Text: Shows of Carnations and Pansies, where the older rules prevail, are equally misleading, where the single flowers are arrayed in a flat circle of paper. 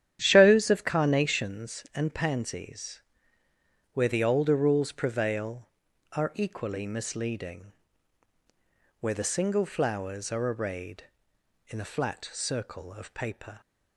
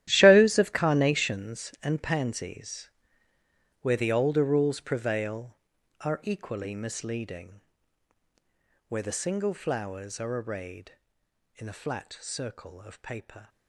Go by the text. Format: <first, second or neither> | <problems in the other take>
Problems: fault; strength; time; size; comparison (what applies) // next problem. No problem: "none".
first | gets quieter; strong; throughout; 15.5 dB // starts louder than the rest; strong; until 1.1 s; 12.5 dB; strong in the first